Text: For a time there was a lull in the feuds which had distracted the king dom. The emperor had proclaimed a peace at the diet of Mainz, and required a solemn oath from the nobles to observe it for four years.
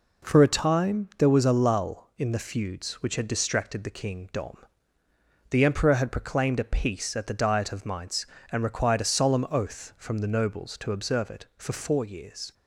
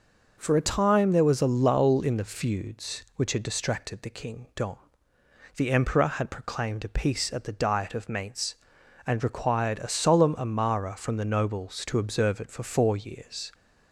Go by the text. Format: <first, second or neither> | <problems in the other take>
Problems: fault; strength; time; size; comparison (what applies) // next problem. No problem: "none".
first | says "amara" for "oath"; at 10.3 s